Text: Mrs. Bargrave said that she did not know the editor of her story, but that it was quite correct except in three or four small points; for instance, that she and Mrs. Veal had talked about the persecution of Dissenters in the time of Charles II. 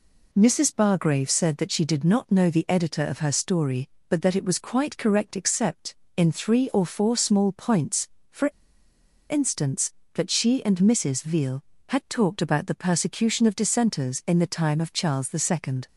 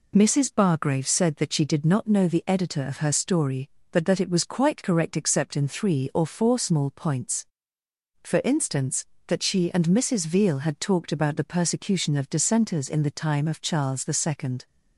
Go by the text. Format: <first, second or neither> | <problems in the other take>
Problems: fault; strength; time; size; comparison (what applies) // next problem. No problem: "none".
second | pauses between "for" and "instance"; noticeable; at 8.4 s; 0.81 s long